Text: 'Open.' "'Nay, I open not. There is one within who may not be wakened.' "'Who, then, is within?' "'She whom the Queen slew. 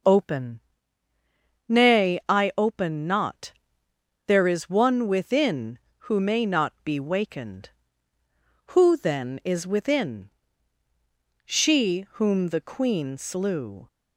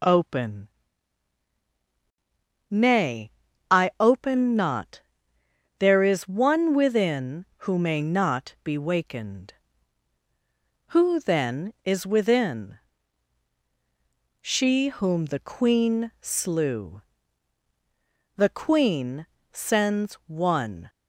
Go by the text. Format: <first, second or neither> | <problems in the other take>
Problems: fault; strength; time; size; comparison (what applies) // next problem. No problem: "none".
first | goes on to say "The Queen sends one"; strong; from 18.3 s on; 2.5 s long